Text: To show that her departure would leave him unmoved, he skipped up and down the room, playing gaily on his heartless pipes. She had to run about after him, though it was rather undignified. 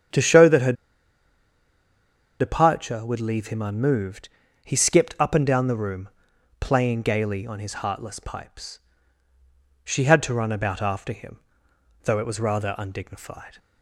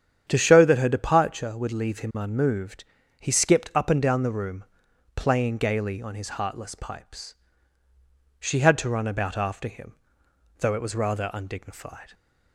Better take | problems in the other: second | starts louder than the rest; strong; until 2.7 s; 8.5 dB; strong in the second // pauses between "her" and "departure"; strong; at 0.7 s; 1.6 s long

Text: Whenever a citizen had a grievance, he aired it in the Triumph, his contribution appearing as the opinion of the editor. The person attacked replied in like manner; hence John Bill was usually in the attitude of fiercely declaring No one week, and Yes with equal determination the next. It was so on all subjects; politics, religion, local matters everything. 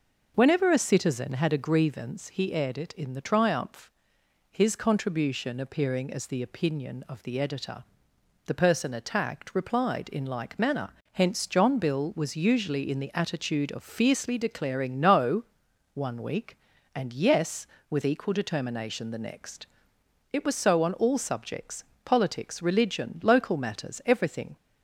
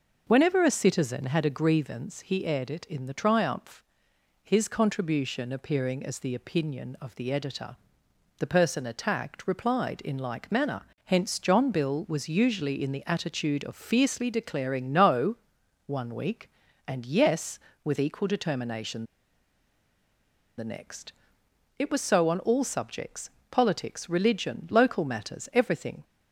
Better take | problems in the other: first | pauses between "No" and "one"; noticeable; at 15.3 s; 0.50 s long; noticeable in the first // pauses between "determination" and "the"; strong; at 19.0 s; 1.5 s long

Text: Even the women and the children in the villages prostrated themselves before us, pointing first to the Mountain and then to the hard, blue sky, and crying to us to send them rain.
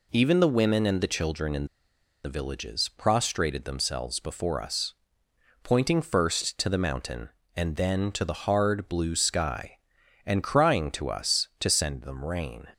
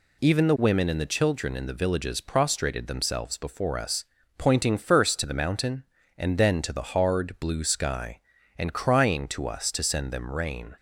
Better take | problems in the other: second | pauses between "in" and "the"; noticeable; at 1.6 s; 0.58 s long

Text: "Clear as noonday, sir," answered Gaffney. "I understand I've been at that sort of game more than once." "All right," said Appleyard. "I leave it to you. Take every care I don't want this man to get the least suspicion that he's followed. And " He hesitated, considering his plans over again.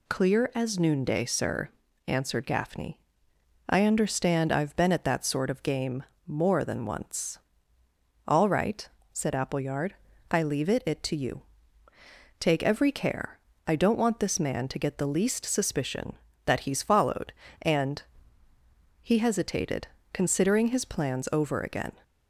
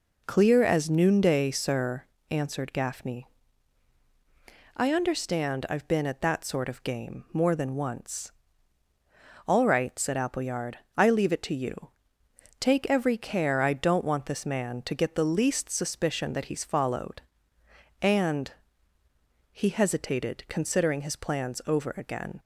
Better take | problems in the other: second | pauses between "game" and "more"; slight; at 6.0 s; 0.24 s long // says "it" twice; at 10.8 s // pauses between "care" and "I"; slight; at 13.3 s; 0.26 s long

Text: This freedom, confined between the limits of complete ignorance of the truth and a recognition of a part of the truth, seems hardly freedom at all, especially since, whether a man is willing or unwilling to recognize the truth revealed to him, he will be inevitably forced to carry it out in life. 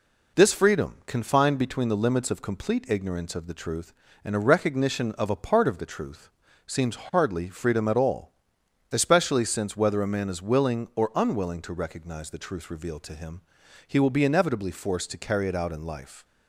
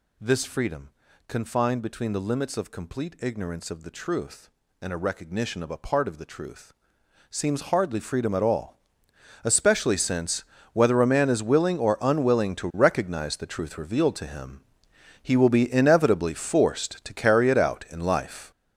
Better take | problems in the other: first | gets louder; strong; throughout; 9 dB

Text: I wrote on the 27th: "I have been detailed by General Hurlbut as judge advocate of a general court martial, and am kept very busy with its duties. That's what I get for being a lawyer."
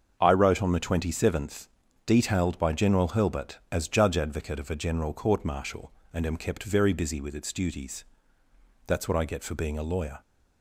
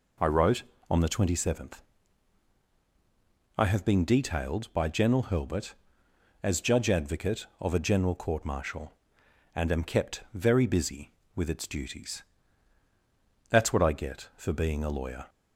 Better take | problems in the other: second | starts louder than the rest; until 1.2 s; 7 dB // skips "I have been"; at 1.8 s

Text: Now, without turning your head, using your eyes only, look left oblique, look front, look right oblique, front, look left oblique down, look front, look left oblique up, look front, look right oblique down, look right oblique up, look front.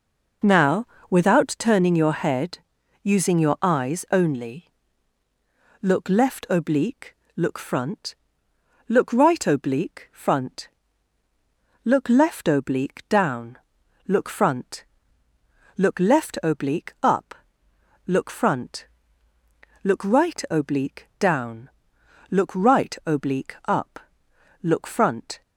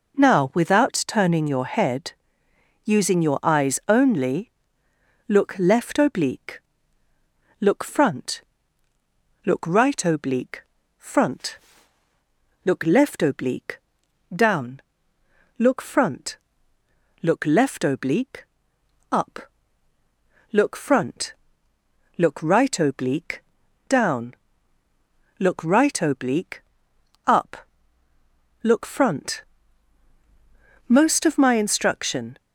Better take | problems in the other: first | pauses between "oblique" and "down"; noticeable; at 13.7 s; 0.56 s long // pauses between "oblique" and "up"; noticeable; at 18.4 s; 0.66 s long // pauses between "oblique" and "down"; noticeable; at 23.4 s; 0.46 s long // pauses between "oblique" and "up"; noticeable; at 26.6 s; 0.66 s long // goes on to say "Most of my instruction"; from 30.8 s on; 1.5 s long

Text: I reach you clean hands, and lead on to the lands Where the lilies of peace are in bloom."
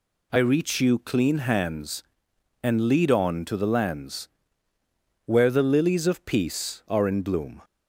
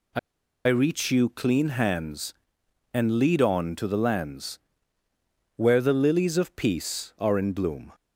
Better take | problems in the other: first | pauses between "I" and "reach"; noticeable; at 0.1 s; 0.48 s long // pauses between "lands" and "Where"; at 4.5 s; 1.0 s long; also in the first

